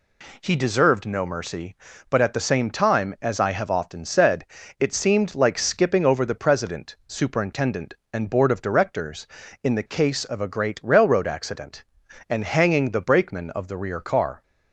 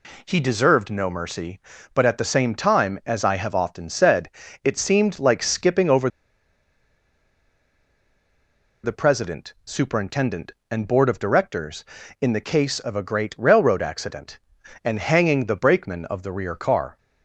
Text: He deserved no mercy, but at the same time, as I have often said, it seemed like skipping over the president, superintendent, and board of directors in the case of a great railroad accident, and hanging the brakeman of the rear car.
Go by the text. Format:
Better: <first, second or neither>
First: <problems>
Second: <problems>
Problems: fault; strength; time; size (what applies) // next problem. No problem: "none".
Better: first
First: none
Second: pauses between "over" and "the"; strong; at 6.0 s; 2.7 s long